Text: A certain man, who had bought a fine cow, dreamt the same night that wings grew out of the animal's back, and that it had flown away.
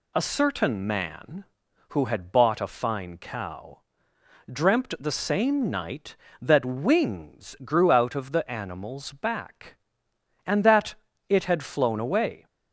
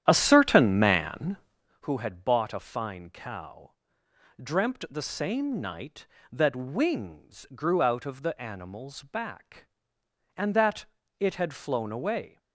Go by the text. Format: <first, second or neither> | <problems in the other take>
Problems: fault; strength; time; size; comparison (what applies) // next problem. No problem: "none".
first | starts louder than the rest; strong; until 1.8 s; 10.5 dB // pauses between "that" and "it"; slight; at 10.8 s; 0.34 s long; slight in the first